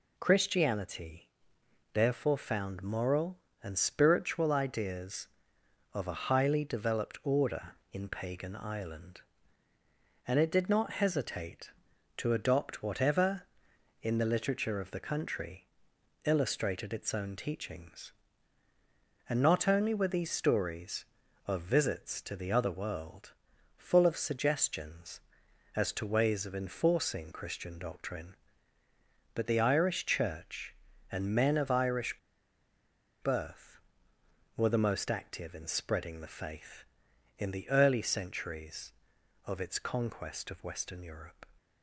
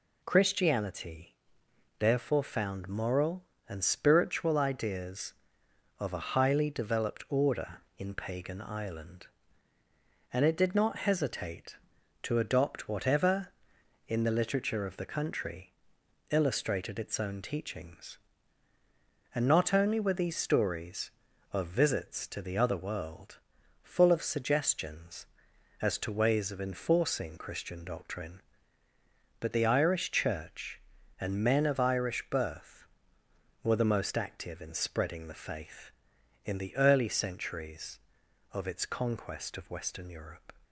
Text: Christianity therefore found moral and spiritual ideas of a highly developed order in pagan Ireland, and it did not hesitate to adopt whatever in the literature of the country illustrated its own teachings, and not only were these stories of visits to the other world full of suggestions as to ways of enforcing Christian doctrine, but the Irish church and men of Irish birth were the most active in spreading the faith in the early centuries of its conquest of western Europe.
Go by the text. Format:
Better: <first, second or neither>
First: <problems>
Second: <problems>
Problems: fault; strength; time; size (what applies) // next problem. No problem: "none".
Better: second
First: pauses between "Christianity" and "therefore"; noticeable; at 1.2 s; 0.64 s long // pauses between "country" and "illustrated"; noticeable; at 15.6 s; 0.58 s long // pauses between "world" and "full"; at 23.3 s; 0.44 s long // pauses between "Irish" and "birth"; at 32.1 s; 1.0 s long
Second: pauses between "Christianity" and "therefore"; noticeable; at 1.3 s; 0.64 s long // pauses between "country" and "illustrated"; noticeable; at 15.7 s; 0.58 s long // pauses between "world" and "full"; at 23.3 s; 0.44 s long